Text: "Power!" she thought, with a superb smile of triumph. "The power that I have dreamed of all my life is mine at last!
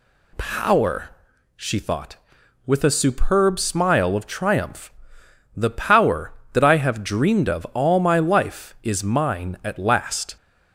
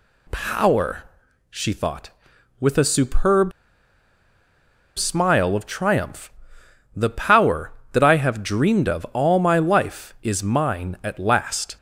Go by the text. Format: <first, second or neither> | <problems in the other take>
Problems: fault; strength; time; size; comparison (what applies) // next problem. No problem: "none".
first | pauses between "superb" and "smile"; strong; at 3.5 s; 1.4 s long